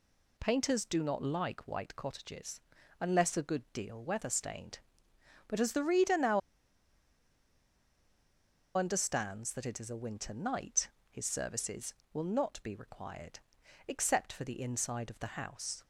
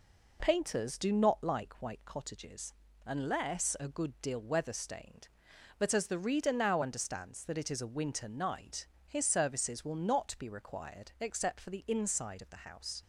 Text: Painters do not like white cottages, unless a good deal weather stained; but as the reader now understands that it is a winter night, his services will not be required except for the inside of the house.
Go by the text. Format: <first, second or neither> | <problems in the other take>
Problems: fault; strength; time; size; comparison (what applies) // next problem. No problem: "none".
second | pauses between "now" and "understands"; strong; at 6.4 s; 2.3 s long // pauses between "required" and "except"; noticeable; at 13.3 s; 0.48 s long